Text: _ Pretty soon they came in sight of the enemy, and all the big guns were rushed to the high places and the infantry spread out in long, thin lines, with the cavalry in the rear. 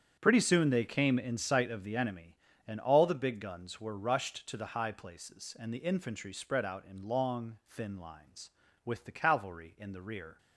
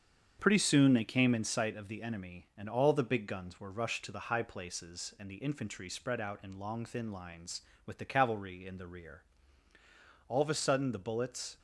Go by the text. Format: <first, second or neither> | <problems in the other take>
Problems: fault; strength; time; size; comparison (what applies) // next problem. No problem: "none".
first | starts louder than the rest; strong; until 1.4 s; 7.5 dB; strong in the first // goes on to say "All of a sudden the bullets"; noticeable; from 10.2 s on; 1.3 s long